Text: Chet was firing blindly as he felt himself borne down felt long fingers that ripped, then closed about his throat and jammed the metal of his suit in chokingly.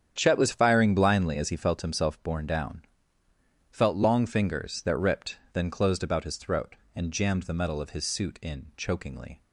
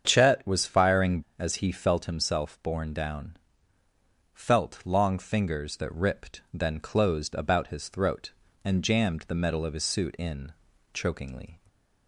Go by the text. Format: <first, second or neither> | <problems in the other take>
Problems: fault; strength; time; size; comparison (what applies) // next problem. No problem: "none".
first | starts louder than the rest; strong; until 1.0 s; 7.5 dB; strong in the first // skips "blindly"; at 1.2 s // pauses between "down" and "felt"; noticeable; at 3.3 s; 0.96 s long; noticeable in the first // pauses between "in" and "chokingly"; at 10.5 s; 0.40 s long // stays silent after the last word; slight; from 11.5 s on; 0.5 s long